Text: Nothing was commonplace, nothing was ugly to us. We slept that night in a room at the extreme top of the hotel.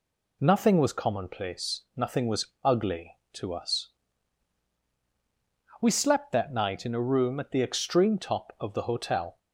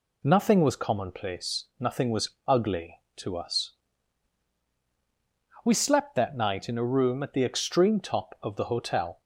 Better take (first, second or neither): neither